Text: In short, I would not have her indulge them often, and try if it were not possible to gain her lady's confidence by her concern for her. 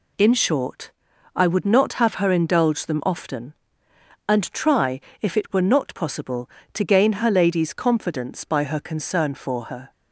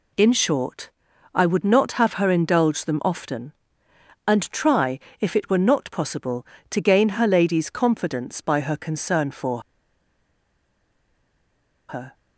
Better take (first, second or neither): first